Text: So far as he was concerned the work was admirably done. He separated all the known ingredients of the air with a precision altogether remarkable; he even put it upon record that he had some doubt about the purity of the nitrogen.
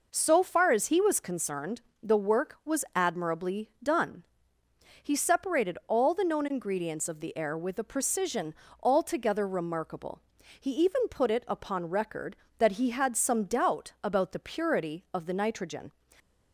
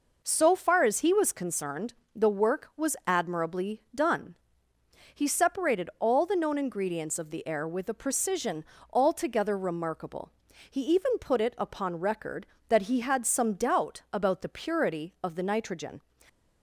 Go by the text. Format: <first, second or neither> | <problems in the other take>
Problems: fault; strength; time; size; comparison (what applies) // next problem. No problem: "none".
neither | pauses between "concerned" and "the"; slight; the same in both // pauses between "precision" and "altogether"; slight; the same in both